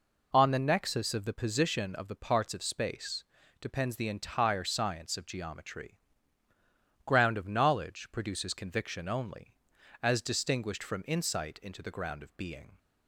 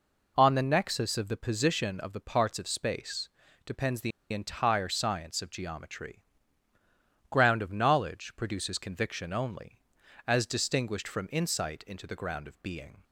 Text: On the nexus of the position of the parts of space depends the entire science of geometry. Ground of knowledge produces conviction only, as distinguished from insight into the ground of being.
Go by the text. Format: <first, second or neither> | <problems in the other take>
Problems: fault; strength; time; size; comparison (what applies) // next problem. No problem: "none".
first | pauses between "space" and "depends"; at 3.2 s; 0.38 s long; also in the first // pauses between "the" and "entire"; slight; at 4.1 s; 0.22 s long